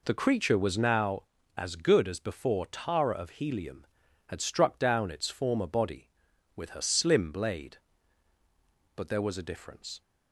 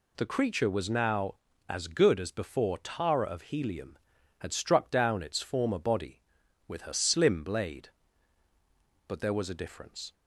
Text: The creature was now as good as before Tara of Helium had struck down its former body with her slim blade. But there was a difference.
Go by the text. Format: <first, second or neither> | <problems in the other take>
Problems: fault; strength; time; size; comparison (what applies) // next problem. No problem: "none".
second | starts louder than the rest; until 1.1 s; 3.5 dB